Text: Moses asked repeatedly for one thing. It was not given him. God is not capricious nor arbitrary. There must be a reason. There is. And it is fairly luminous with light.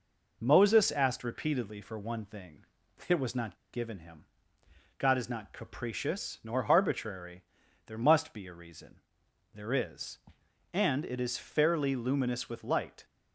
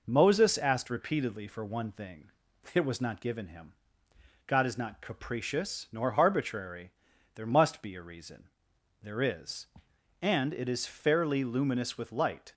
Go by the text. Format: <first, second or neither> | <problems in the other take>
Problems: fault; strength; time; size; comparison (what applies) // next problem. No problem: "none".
second | pauses between "not" and "given"; slight; at 3.5 s; 0.16 s long